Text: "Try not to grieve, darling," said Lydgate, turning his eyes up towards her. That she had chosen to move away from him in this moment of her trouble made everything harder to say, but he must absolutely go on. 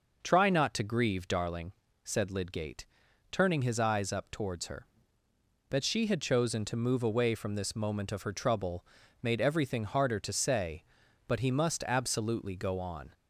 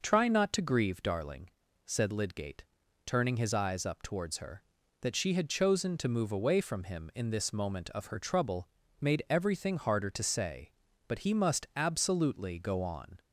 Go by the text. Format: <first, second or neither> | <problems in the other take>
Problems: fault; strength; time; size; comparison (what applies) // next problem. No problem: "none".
second | skips "him in"; at 7.5 s // pauses between "trouble" and "made"; at 8.8 s; 0.38 s long; slight in the second